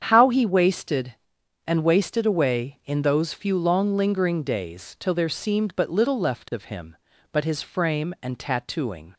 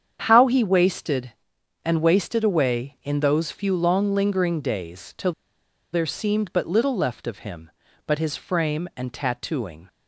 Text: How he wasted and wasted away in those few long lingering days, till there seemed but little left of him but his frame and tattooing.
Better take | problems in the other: first | starts louder than the rest; strong; until 1.2 s; 8 dB; strong in the first // pauses between "till" and "there"; noticeable; at 5.3 s; 0.60 s long

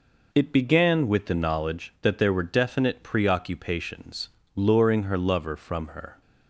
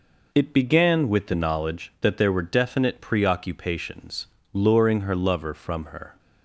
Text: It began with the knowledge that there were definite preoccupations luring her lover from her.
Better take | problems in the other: neither | pauses between "preoccupations" and "luring"; slight; the same in both

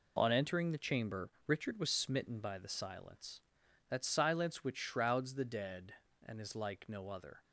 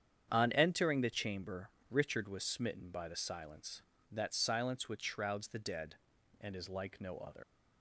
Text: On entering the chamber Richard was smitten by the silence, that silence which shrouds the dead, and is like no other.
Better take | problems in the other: first | starts louder than the rest; strong; until 1.3 s; 8.5 dB // pauses between "chamber" and "Richard"; slight; at 1.7 s; 0.18 s long; slight in the first // leaves "other" unfinished; at 7.4 s; 120 ms

